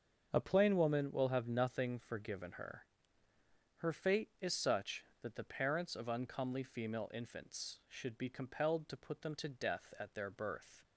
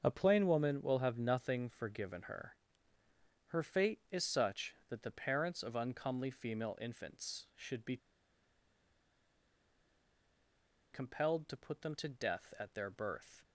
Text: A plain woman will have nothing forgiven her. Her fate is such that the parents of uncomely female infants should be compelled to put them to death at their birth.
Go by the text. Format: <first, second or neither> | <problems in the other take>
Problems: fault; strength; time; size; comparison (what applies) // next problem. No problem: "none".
first | starts louder than the rest; until 1.0 s; 7 dB; also in the first // pauses between "be" and "compelled"; strong; at 7.9 s; 2.9 s long